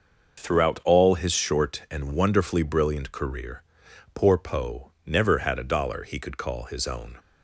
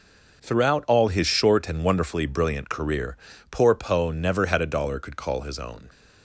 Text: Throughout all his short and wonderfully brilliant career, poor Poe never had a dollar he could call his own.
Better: first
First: none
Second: skips "he"; at 4.9 s

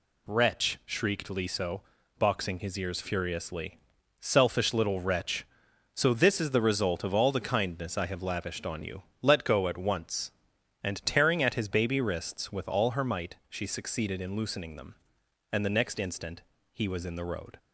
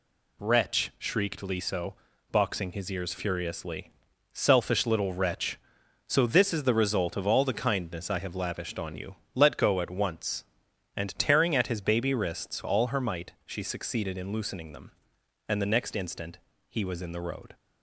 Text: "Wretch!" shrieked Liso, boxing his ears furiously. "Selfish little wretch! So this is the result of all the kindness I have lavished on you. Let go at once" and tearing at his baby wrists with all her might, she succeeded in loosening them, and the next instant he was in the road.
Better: first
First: pauses between "instant" and "he"; slight; at 16.4 s; 0.30 s long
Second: skips "with"; at 12.6 s // pauses between "instant" and "he"; slight; at 16.3 s; 0.30 s long

